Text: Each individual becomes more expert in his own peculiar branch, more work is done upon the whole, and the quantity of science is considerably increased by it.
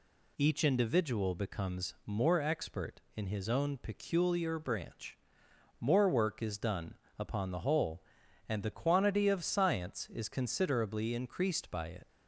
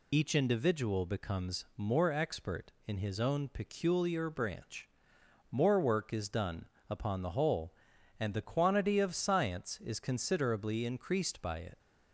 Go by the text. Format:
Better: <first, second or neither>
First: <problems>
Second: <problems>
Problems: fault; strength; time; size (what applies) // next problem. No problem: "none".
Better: first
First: pauses between "done" and "upon"; slight; at 6.9 s; 0.24 s long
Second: loses the start of "Each"; at 0.1 s; 45 ms // pauses between "done" and "upon"; slight; at 6.6 s; 0.24 s long